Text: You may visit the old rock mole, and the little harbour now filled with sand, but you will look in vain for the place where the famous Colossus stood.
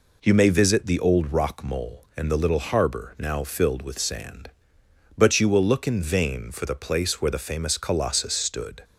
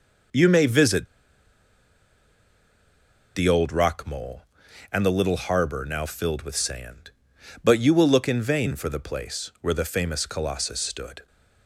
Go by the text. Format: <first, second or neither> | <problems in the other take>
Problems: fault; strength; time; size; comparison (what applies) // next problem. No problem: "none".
first | pauses between "visit" and "the"; strong; at 1.0 s; 2.2 s long